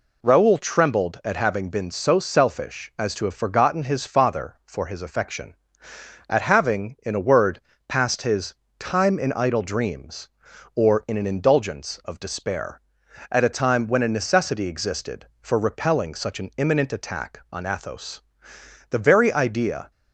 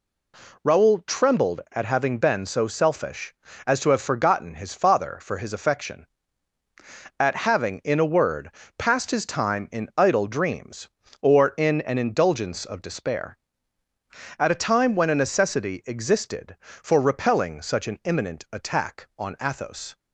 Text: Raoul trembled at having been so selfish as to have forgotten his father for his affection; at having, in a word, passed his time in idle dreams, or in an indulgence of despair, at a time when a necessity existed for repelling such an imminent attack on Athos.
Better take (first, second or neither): second